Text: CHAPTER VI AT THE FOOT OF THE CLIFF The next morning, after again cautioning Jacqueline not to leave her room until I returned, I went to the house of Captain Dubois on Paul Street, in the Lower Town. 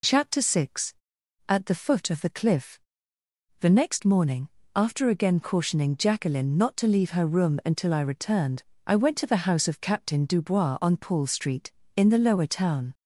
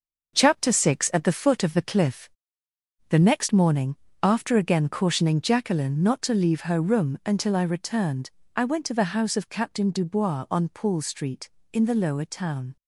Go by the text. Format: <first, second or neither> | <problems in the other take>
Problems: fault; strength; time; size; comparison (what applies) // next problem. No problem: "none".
first | gets quieter; strong; throughout; 7.5 dB // pauses between "CLIFF" and "The"; noticeable; at 2.2 s; 0.82 s long; noticeable in the first